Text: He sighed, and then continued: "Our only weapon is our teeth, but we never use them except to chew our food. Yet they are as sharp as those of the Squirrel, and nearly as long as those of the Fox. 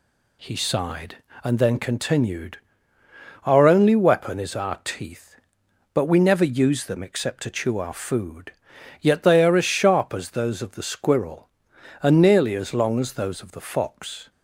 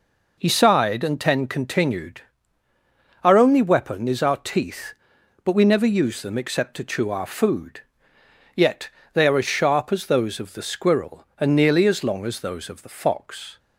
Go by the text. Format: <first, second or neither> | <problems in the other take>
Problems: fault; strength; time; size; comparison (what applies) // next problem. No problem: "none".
first | says "ten" for "then"; at 1.1 s // pauses between "Yet" and "they"; slight; at 8.8 s; 0.26 s long